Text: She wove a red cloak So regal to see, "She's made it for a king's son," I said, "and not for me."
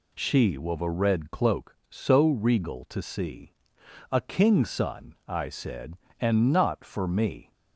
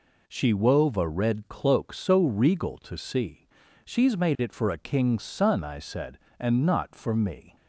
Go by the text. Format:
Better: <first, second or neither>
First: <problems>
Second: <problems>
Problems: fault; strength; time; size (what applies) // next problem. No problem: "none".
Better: second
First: skips "She's made it for"; at 3.8 s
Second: none